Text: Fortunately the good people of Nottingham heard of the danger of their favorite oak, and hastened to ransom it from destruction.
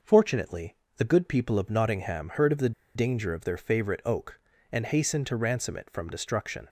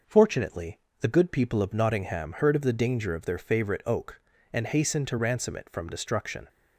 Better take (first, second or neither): second